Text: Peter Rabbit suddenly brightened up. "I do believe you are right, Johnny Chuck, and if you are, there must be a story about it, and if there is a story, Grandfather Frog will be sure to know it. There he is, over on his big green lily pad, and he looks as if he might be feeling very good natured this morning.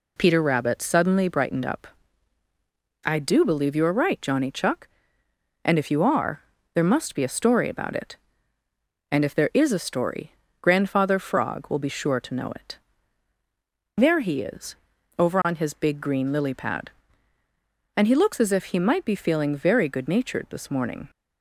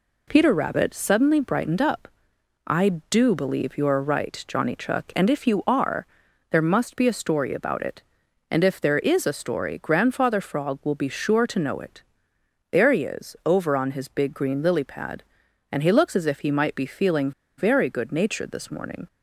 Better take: first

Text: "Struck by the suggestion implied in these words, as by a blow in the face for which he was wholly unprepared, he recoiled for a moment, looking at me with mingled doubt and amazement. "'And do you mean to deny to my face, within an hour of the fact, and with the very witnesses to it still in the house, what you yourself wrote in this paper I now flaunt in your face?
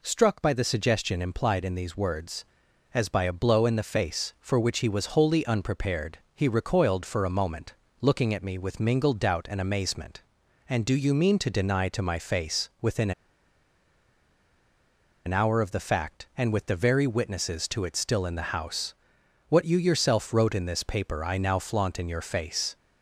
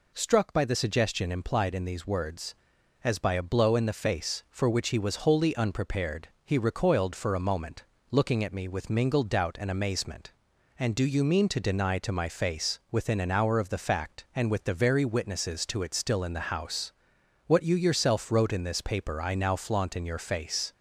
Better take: second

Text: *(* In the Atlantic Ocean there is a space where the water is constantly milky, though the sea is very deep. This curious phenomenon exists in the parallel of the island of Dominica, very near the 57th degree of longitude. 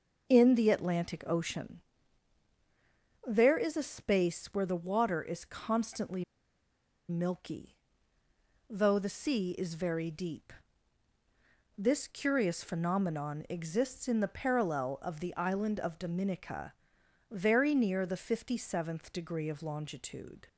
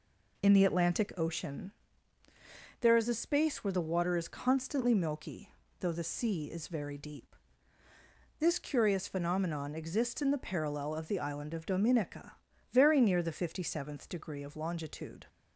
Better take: second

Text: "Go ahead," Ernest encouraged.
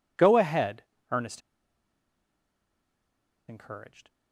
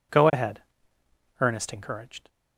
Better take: second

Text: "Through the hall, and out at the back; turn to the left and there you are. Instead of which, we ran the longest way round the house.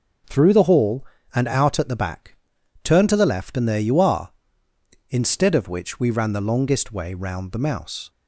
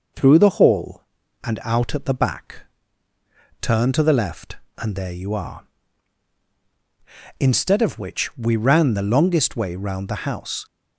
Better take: second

